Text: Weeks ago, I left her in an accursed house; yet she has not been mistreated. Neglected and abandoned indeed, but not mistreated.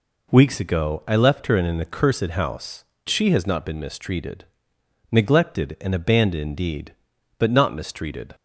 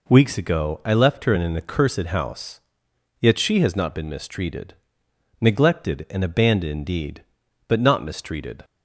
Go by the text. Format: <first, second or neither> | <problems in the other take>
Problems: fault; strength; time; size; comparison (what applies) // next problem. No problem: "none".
second | skips "yet"; at 2.9 s